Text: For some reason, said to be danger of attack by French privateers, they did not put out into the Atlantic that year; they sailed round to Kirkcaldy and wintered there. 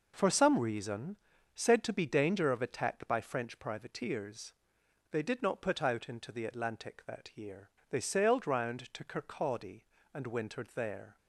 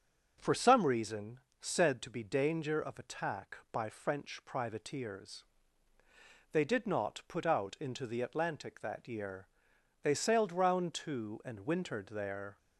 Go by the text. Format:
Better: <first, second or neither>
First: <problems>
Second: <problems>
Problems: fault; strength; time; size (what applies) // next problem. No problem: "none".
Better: first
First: none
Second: starts louder than the rest; until 1.3 s; 6 dB // skips "Kirkcaldy"; at 11.4 s